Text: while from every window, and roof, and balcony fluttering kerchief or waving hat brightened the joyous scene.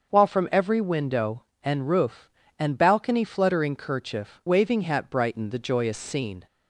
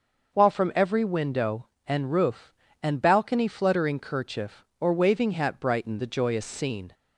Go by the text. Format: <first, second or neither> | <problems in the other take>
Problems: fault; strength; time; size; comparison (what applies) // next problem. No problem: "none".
second | starts louder than the rest; until 1.1 s; 6.5 dB // skips "or"; at 4.4 s